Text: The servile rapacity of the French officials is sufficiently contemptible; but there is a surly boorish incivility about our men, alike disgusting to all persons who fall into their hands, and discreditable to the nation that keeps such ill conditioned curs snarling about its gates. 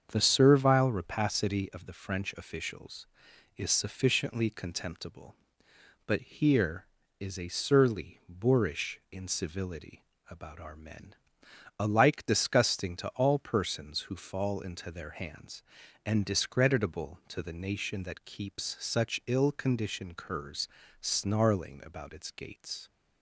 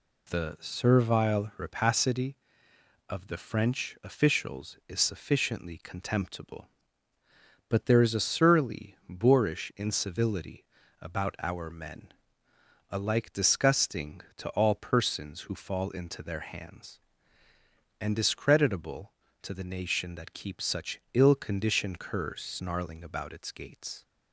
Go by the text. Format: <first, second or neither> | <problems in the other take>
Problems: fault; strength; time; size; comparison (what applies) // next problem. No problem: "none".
second | starts louder than the rest; strong; until 1.0 s; 7 dB // says "here" for "there"; at 6.2 s // pauses between "incivility" and "about"; slight; at 10.0 s; 0.26 s long; slight in the second // pauses between "curs" and "snarling"; slight; at 20.6 s; 0.32 s long